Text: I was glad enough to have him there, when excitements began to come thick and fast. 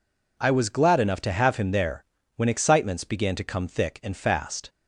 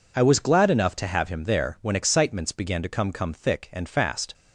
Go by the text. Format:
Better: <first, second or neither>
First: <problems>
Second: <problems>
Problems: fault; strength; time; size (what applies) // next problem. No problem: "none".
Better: first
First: none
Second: says "come" twice; at 3.1 s